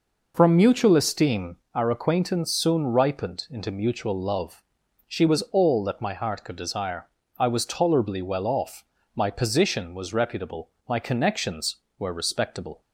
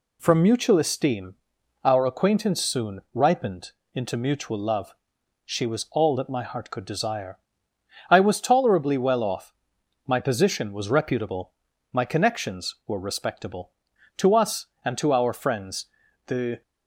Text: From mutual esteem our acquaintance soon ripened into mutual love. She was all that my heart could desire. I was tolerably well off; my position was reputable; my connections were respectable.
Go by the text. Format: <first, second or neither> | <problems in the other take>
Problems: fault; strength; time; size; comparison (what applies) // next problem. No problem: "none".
first | pauses between "esteem" and "our"; noticeable; at 1.3 s; 0.50 s long; slight in the first // pauses between "ripened" and "into"; slight; at 3.7 s; 0.24 s long // goes on to say "To us and to our friends the"; strong; from 14.1 s on; 2.4 s long